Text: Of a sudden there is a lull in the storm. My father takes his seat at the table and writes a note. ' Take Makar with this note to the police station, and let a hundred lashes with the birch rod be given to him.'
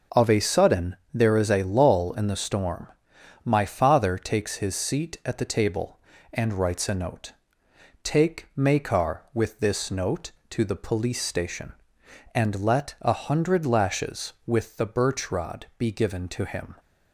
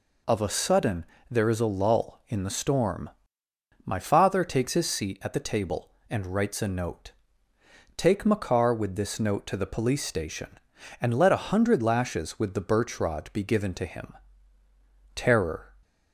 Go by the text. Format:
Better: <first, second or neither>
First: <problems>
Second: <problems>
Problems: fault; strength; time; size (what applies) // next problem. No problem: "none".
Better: first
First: pauses between "sudden" and "there"; slight; at 0.9 s; 0.16 s long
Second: pauses between "sudden" and "there"; slight; at 1.0 s; 0.26 s long // goes on to say "Terror"; from 15.1 s on; 0.58 s long